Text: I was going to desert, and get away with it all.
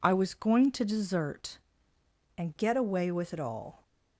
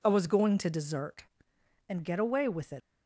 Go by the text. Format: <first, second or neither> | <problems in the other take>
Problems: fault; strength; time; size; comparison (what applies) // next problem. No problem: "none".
first | stops before "all"; at 2.8 s